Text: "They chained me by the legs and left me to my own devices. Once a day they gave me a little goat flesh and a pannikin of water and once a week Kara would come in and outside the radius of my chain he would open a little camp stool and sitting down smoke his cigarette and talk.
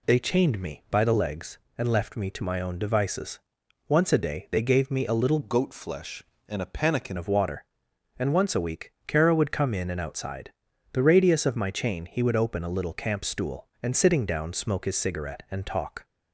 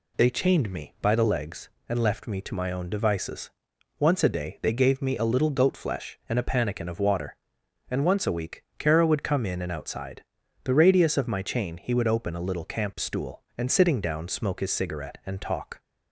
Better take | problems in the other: second | changes voice from "goat" to "pannikin"; from 5.4 to 7.1 s; 1.7 s long // pauses between "outside" and "the"; at 10.5 s; 0.42 s long; also in the second

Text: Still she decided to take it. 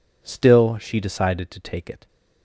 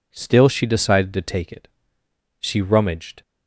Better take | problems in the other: first | goes on to say "She rummaged"; noticeable; from 2.3 s on; 0.82 s long

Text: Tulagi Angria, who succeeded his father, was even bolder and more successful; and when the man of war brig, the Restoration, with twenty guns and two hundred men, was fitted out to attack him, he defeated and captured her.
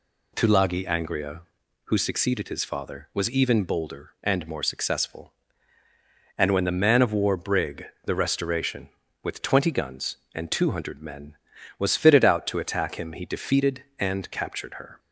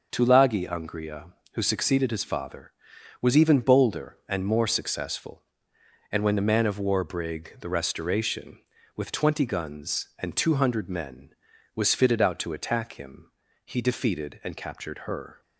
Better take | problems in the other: neither | none

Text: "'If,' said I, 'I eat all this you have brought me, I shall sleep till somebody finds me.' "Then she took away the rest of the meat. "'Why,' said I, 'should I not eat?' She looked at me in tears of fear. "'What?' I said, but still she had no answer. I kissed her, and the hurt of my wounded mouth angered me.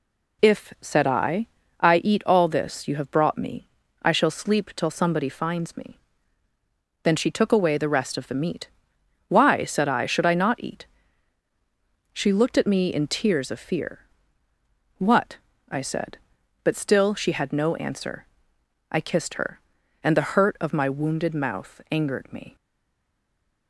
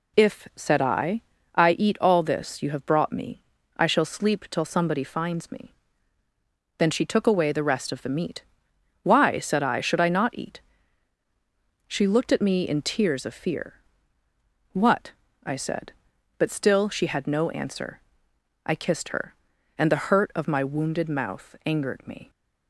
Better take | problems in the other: second | stays silent after the last word; from 22.5 s on; 1.1 s long

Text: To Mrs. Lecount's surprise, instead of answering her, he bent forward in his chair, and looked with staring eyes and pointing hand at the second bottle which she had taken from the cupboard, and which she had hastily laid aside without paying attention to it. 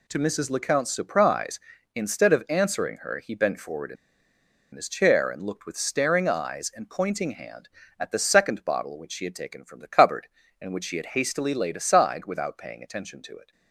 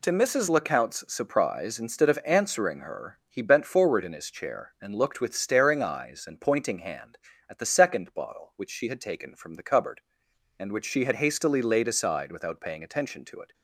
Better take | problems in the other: second | pauses between "in" and "his"; noticeable; at 3.9 s; 0.79 s long

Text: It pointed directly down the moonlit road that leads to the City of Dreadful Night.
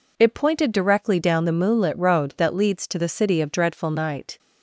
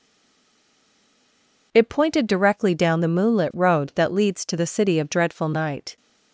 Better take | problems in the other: first | stays silent before the first word; noticeable; until 1.7 s; 1.7 s long

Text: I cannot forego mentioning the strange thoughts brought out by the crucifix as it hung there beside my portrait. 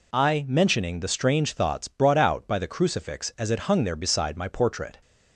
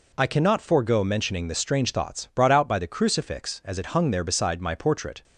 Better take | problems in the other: second | skips "cannot forego"; at 0.4 s

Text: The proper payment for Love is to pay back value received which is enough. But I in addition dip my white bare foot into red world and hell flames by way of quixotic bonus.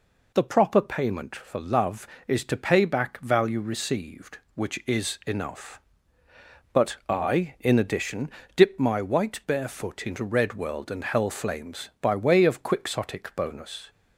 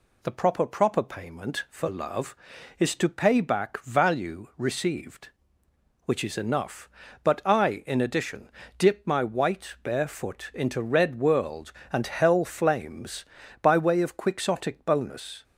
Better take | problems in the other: first | says "proper" twice; at 0.6 s // pauses between "addition" and "dip"; slight; at 8.5 s; 0.26 s long; slight in the first

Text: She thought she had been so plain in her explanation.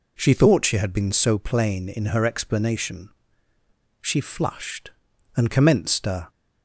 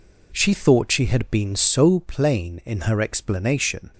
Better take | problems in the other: second | goes on to say "She flushed and commenced a"; strong; from 4.0 s on; 2.2 s long

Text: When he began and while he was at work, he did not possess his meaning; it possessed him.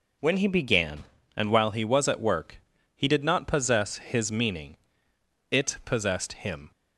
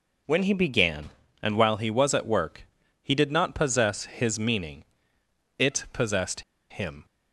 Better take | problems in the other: first | pauses between "possessed" and "him"; slight; at 6.4 s; 0.29 s long

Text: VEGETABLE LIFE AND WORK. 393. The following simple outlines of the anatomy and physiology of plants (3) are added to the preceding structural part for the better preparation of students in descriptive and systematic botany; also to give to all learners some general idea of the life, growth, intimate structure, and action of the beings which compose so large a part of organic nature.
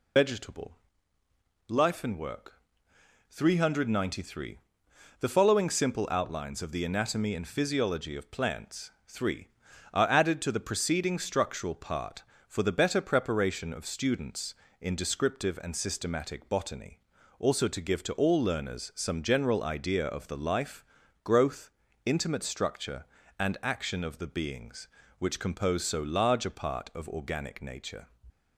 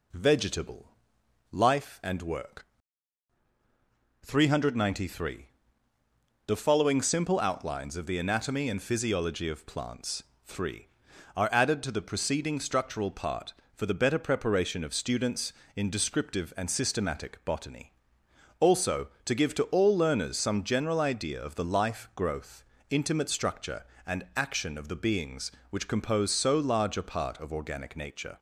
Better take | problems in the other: second | loses the start of "VEGETABLE"; at 0.1 s; 105 ms // pauses between "VEGETABLE" and "LIFE"; noticeable; at 0.7 s; 0.94 s long; noticeable in the second

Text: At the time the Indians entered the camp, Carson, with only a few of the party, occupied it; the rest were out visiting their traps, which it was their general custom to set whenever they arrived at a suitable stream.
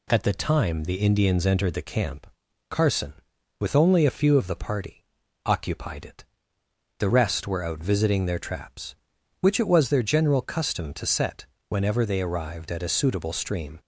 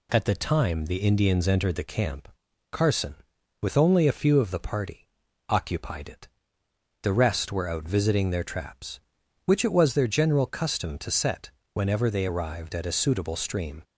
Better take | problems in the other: neither | pauses between "set" and "whenever"; slight; the same in both

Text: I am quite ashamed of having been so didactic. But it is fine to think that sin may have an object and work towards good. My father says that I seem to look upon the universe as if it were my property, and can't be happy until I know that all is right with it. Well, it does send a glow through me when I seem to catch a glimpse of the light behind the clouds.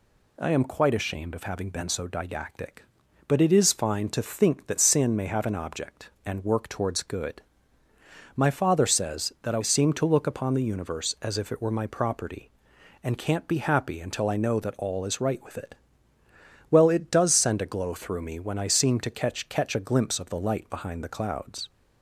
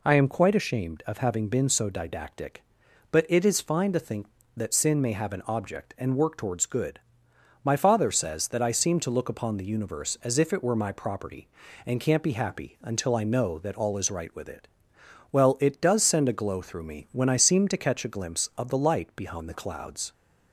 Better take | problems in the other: second | says "catch" twice; at 19.4 s

